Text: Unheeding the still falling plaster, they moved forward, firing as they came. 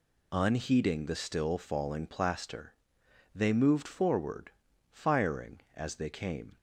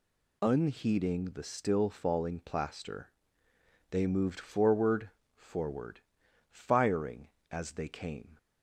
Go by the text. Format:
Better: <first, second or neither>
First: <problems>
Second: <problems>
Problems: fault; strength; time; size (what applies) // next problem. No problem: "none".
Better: first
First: none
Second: says "forward" twice; at 5.3 s